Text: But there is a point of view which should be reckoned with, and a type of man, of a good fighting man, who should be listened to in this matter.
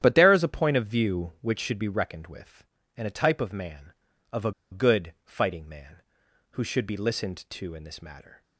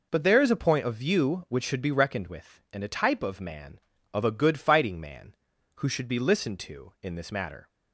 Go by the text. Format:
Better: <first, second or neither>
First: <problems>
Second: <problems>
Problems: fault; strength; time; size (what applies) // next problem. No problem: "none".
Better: second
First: starts louder than the rest; strong; until 1.0 s; 10.5 dB // pauses between "a" and "good"; slight; at 4.5 s; 0.21 s long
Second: none